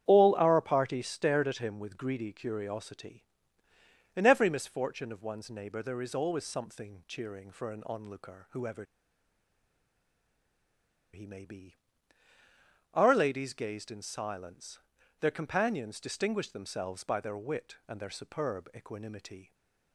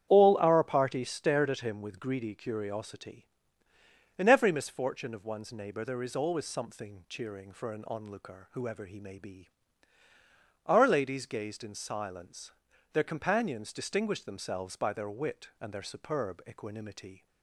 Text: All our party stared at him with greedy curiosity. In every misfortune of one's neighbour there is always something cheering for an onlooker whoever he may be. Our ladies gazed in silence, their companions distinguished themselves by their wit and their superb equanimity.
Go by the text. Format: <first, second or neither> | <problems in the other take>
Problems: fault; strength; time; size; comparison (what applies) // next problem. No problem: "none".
second | starts louder than the rest; strong; until 1.1 s; 9 dB; strong in the second // pauses between "whoever" and "he"; strong; at 8.8 s; 2.2 s long